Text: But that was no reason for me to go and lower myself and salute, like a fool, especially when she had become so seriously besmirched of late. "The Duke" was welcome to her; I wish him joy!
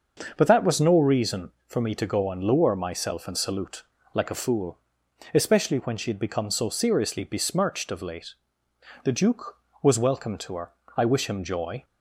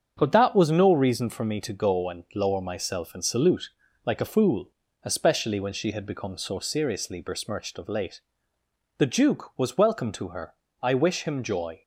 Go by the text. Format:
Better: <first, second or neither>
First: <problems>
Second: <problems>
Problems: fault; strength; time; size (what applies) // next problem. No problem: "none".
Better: neither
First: starts louder than the rest; until 1.3 s; 6 dB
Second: starts louder than the rest; strong; until 1.1 s; 7.5 dB